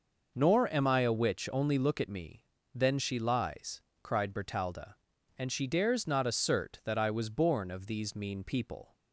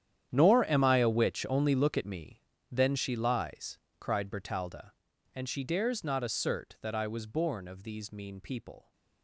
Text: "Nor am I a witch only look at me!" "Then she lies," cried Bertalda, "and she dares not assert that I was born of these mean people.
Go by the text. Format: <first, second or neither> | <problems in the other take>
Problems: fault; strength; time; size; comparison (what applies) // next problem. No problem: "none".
first | gets quieter; strong; throughout; 17 dB